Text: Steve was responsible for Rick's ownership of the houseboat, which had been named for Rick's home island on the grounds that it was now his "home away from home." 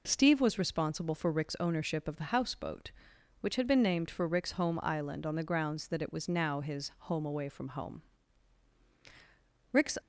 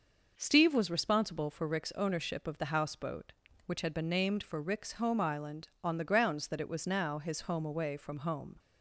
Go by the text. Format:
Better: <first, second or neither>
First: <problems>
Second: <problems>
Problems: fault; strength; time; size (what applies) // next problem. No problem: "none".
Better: second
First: goes on to say "Rick's"; slight; from 9.7 s on; 0.26 s long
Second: none